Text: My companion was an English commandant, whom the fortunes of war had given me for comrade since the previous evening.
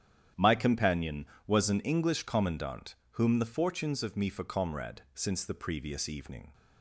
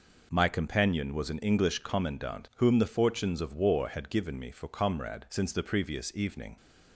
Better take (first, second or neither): second